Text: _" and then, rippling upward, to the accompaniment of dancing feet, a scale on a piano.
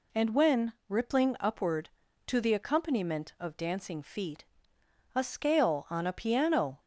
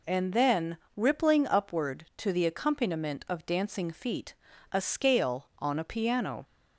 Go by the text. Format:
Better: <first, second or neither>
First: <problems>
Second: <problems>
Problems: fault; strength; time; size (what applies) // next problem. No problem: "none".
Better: second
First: says "when" for "then"; at 0.3 s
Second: none